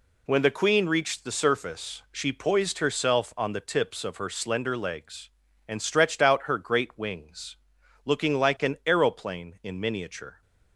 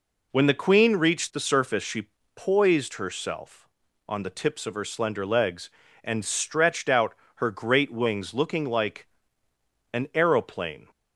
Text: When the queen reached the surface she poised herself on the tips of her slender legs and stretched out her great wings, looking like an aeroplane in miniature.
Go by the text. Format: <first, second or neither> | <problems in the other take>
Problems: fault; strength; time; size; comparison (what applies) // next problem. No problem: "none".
first | pauses between "she" and "poised"; slight; at 2.0 s; 0.28 s long // pauses between "out" and "her"; slight; at 7.1 s; 0.22 s long // pauses between "like" and "an"; noticeable; at 9.0 s; 0.86 s long // stops before "in miniature"; at 10.9 s